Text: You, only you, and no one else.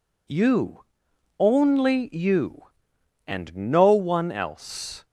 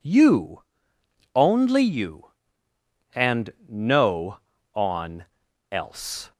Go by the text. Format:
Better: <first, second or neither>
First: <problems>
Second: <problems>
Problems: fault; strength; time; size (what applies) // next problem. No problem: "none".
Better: first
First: none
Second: pauses between "and" and "no"; slight; at 3.5 s; 0.16 s long // says "on" for "one"; at 4.7 s